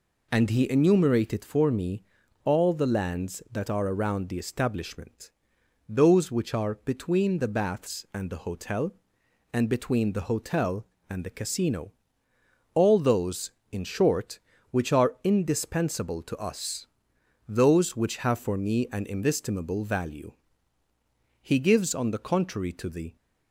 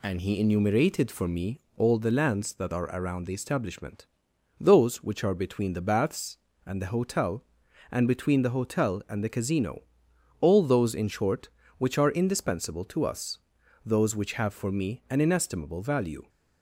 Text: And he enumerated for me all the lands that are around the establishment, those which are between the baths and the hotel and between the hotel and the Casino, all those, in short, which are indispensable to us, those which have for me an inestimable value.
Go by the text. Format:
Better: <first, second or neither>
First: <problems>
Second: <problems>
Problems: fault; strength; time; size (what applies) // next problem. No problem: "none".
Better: second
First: pauses between "me" and "all"; at 2.0 s; 0.42 s long // goes on to say "He gives on the contrary to the"; strong; from 21.4 s on; 1.7 s long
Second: pauses between "me" and "all"; slight; at 1.6 s; 0.16 s long